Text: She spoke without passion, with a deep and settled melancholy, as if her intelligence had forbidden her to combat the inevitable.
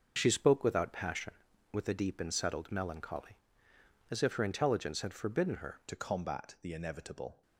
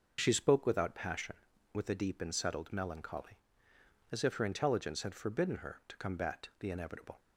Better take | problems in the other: second | starts louder than the rest; until 1.1 s; 6.5 dB; noticeable in the second // changes voice at "to"; from 5.8 s on; 1.6 s long

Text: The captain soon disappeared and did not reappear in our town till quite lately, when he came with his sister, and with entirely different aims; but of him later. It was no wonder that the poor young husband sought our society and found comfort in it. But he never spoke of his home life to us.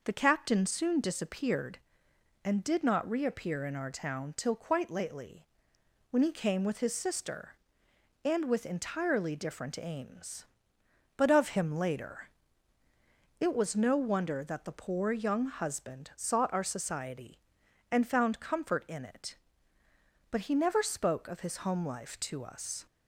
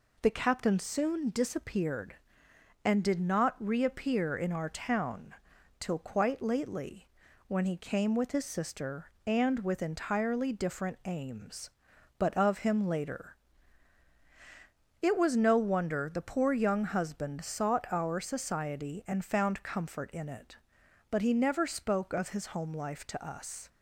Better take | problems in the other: first | pauses between "town" and "till"; noticeable; at 5.3 s; 0.46 s long // skips "that"; at 16.1 s

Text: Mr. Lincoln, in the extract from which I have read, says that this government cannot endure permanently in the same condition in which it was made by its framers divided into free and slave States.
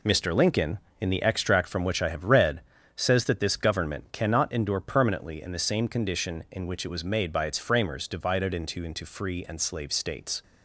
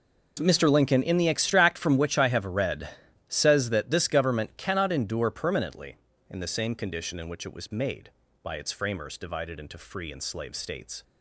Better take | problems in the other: second | says "into" twice; at 8.8 s

